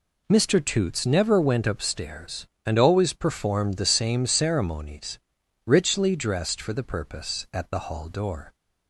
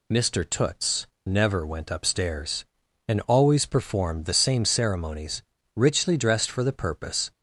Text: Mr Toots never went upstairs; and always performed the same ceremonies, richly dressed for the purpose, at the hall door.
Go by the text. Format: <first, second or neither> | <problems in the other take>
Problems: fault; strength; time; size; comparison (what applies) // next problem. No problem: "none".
first | pauses between "Toots" and "never"; slight; at 1.0 s; 0.18 s long // stops before "at the hall door"; at 7.3 s